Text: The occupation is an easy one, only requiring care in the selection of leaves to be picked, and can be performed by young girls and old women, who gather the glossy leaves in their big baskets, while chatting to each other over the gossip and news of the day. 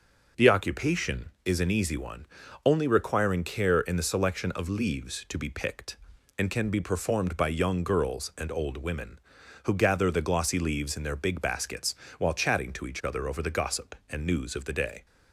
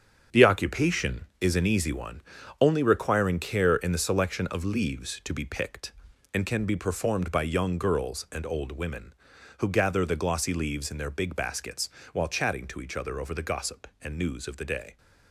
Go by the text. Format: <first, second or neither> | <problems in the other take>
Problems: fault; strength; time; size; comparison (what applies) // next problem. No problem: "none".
first | gets quieter; strong; throughout; 9 dB